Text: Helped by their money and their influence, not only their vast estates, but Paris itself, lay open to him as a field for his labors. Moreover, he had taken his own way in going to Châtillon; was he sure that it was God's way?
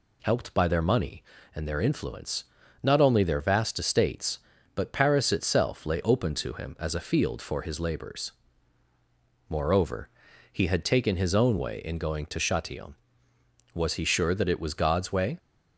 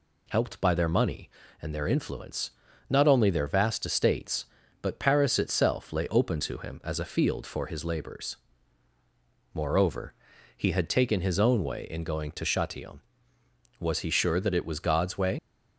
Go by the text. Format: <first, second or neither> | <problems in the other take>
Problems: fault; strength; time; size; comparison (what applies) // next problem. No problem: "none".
first | leaves "way" unfinished; at 15.3 s; 50 ms